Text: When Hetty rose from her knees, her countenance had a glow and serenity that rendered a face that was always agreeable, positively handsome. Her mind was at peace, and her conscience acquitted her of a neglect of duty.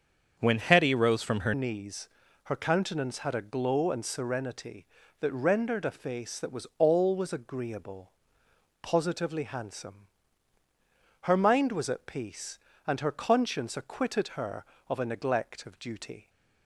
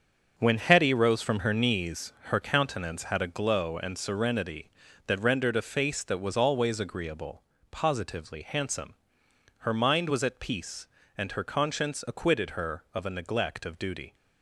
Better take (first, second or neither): second